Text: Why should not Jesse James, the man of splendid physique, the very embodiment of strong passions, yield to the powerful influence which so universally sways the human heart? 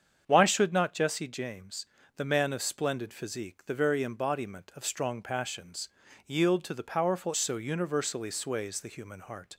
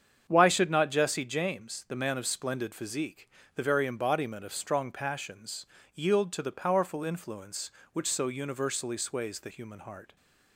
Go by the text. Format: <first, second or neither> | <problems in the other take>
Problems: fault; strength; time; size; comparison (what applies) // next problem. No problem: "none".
second | starts louder than the rest; strong; until 1.2 s; 7.5 dB; strong in the second // skips "influence which"; at 7.3 s